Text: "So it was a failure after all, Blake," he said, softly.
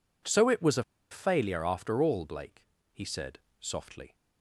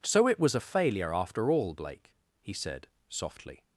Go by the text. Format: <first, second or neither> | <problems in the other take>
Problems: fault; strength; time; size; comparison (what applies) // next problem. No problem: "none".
second | pauses between "a" and "failure"; slight; at 0.8 s; 0.27 s long